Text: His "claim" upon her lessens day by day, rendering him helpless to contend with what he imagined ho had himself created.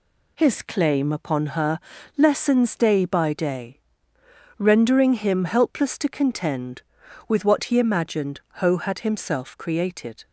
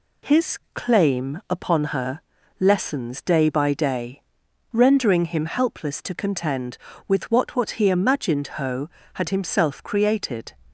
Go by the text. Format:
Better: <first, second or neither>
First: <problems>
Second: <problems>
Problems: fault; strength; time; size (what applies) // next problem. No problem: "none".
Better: first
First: pauses between "her" and "lessens"; at 1.7 s; 0.38 s long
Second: pauses between "her" and "lessens"; slight; at 2.2 s; 0.36 s long // says "what" twice; at 7.5 s